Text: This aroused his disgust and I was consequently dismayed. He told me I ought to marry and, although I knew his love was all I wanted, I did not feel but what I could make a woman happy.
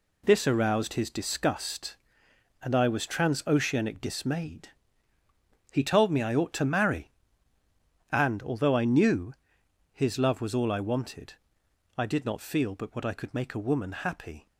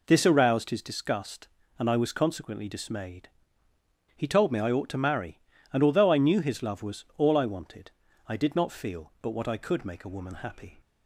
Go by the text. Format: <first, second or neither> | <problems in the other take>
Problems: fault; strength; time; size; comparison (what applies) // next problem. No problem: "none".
second | says "transoceanic" for "consequently"; at 3.0 s // pauses between "knew" and "his"; noticeable; at 9.3 s; 0.60 s long